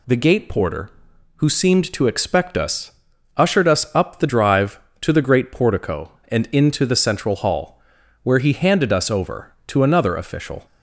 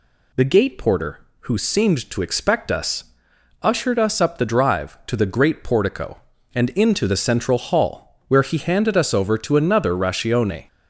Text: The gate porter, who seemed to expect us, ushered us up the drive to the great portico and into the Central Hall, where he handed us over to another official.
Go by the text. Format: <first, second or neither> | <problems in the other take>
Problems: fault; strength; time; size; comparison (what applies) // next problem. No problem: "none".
first | says "ratione" for "official"; at 9.9 s